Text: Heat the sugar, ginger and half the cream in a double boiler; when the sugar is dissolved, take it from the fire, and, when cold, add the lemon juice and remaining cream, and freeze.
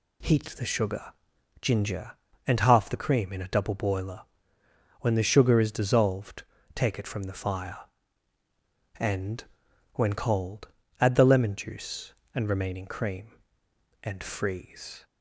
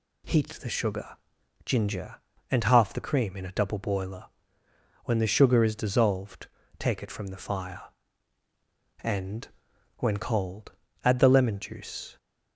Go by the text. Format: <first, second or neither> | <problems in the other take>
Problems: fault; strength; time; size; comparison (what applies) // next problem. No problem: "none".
first | stops before "and remaining cream and freeze"; at 12.1 s